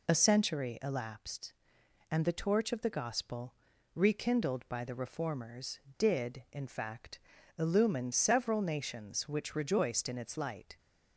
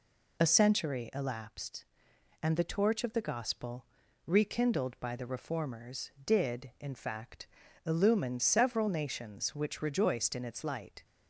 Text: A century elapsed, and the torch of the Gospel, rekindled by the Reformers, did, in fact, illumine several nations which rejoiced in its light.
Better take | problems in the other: neither | none

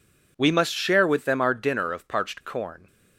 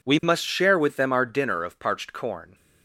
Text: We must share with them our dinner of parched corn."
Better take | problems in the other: neither | none

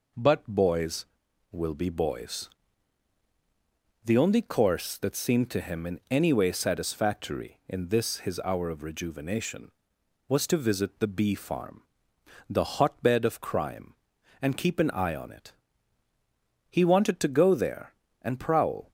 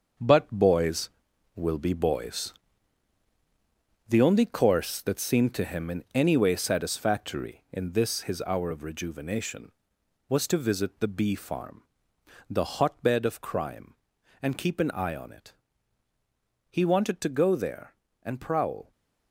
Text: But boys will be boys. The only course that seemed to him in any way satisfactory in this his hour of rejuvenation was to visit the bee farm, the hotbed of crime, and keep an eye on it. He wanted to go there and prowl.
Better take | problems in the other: first | gets quieter; strong; throughout; 8 dB

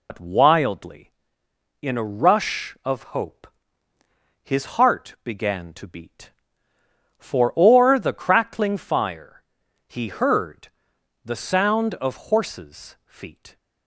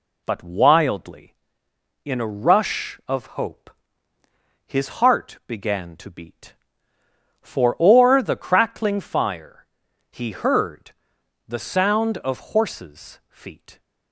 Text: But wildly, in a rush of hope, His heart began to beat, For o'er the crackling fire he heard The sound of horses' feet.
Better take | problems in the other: second | loses the start of "But"; at 0.0 s; 80 ms // pauses between "fire" and "he"; noticeable; at 9.4 s; 0.48 s long; noticeable in the second // pauses between "heard" and "The"; noticeable; at 10.6 s; 0.56 s long; noticeable in the second

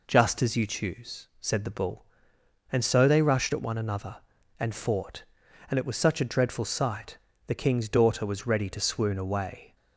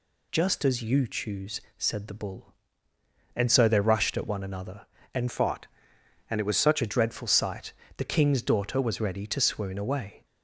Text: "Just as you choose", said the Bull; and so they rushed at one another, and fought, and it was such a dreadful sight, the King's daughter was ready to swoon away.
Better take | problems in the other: first | changes voice from "fought" to "such"; from 5.2 to 6.8 s; 1.6 s long

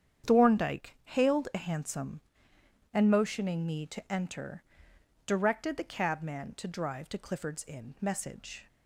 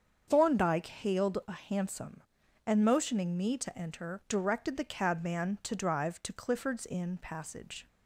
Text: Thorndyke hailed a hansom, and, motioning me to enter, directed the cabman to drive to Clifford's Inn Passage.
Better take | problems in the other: second | starts louder than the rest; strong; until 1.3 s; 8.5 dB; strong in the second // says "Message" for "Passage"; at 8.0 s

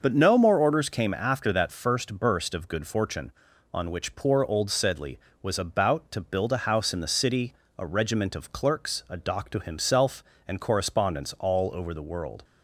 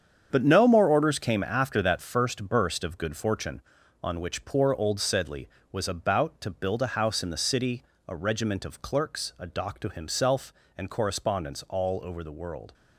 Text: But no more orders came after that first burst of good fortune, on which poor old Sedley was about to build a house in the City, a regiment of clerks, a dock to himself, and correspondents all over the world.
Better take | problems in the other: first | gets quieter; strong; throughout; 10 dB // starts louder than the rest; strong; until 1.3 s; 8 dB; noticeable in the first

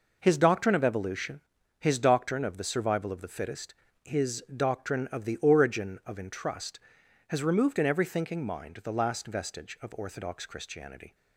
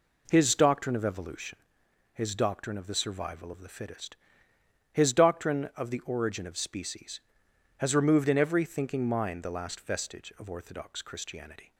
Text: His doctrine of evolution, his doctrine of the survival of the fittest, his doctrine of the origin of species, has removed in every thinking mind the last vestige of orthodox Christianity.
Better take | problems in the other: second | says "entrust" for "species"; at 6.1 s

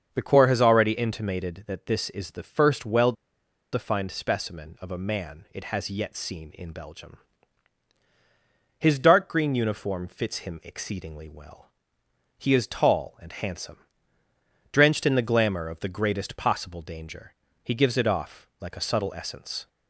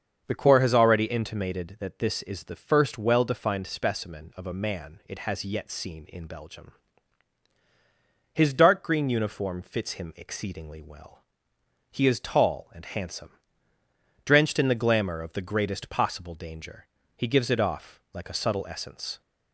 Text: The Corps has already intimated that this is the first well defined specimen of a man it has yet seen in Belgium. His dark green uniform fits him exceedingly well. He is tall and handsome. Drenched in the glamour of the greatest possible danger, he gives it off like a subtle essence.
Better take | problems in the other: second | starts louder than the rest; until 1.1 s; 7 dB; also in the second // pauses between "well" and "defined"; noticeable; at 3.1 s; 0.59 s long

